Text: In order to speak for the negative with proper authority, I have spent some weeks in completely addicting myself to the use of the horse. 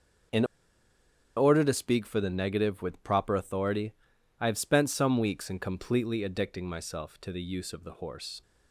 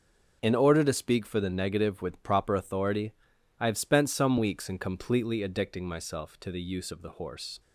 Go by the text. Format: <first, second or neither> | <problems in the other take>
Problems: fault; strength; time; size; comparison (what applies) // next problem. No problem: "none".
second | pauses between "In" and "order"; noticeable; at 0.4 s; 0.93 s long